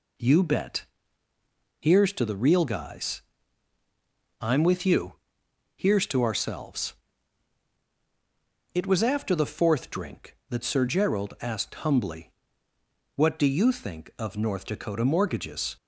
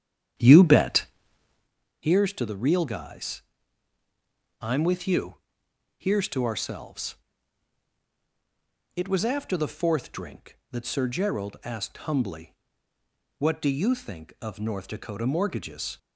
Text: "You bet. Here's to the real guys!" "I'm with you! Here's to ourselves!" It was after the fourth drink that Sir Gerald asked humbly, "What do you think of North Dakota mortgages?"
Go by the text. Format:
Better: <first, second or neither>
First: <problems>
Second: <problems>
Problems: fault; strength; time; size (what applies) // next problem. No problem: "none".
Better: first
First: none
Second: starts louder than the rest; strong; until 1.7 s; 9 dB